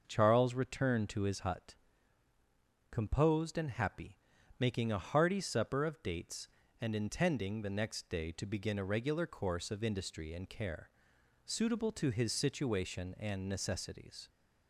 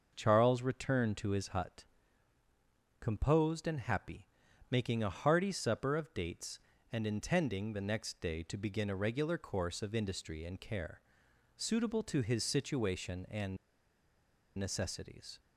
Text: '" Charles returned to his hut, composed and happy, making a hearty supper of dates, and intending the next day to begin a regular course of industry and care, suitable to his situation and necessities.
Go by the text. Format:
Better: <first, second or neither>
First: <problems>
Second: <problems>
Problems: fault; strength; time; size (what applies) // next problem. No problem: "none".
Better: first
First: starts louder than the rest; until 1.0 s; 6 dB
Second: starts louder than the rest; noticeable; until 1.1 s; 6 dB // pauses between "and" and "necessities"; at 13.5 s; 1.0 s long